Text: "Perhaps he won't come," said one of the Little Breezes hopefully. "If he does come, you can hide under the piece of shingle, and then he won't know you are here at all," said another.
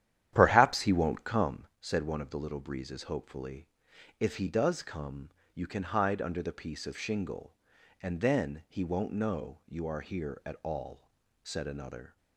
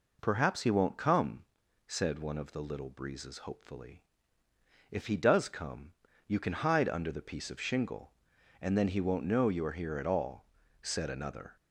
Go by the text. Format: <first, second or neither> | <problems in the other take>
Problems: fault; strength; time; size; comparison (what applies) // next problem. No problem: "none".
second | starts louder than the rest; strong; until 1.6 s; 11 dB